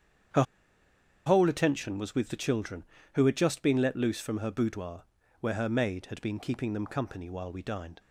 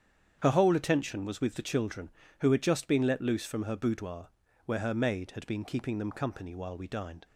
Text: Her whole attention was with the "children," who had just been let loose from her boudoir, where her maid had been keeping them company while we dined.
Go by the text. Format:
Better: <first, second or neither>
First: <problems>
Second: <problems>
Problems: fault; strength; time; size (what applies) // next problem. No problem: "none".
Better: second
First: starts louder than the rest; strong; until 2.1 s; 8.5 dB // pauses between "Her" and "whole"; noticeable; at 0.4 s; 0.83 s long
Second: starts louder than the rest; strong; until 1.4 s; 8.5 dB